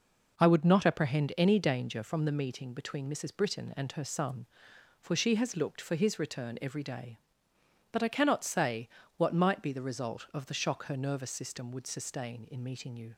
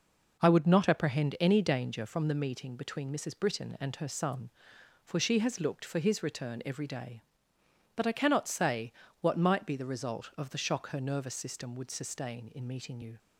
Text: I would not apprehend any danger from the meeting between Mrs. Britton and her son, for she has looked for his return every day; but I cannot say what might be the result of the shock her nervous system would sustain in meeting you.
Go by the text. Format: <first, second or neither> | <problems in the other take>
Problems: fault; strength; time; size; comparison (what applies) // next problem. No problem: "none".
neither | pauses between "say" and "what"; slight; the same in both